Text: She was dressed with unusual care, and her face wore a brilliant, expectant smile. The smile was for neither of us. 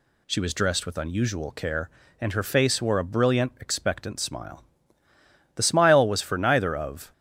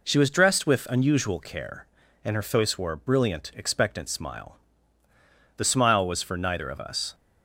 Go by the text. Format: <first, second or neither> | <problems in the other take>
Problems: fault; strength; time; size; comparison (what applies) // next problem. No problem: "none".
second | stops before "us"; at 7.1 s